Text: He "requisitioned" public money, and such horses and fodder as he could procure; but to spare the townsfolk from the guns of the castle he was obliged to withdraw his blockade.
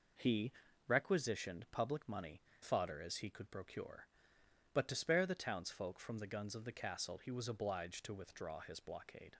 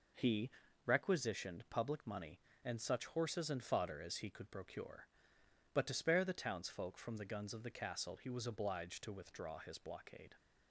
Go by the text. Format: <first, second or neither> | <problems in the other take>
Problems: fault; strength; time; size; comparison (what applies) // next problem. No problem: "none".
second | pauses between "He" and "requisitioned"; slight; at 0.5 s; 0.34 s long; slight in the second // skips "and such horses and"; at 2.5 s